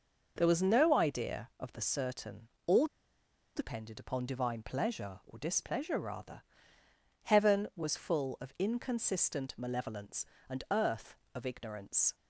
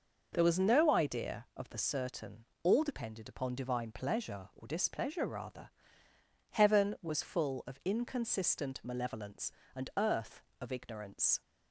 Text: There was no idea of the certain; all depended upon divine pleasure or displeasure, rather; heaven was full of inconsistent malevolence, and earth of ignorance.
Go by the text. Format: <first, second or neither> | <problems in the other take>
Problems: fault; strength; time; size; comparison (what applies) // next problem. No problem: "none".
second | pauses between "all" and "depended"; noticeable; at 2.8 s; 0.70 s long